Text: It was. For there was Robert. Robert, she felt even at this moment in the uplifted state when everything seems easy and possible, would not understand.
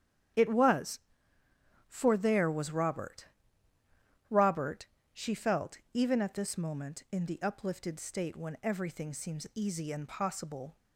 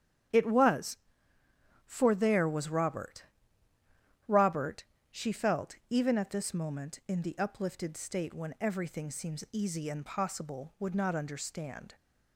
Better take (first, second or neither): second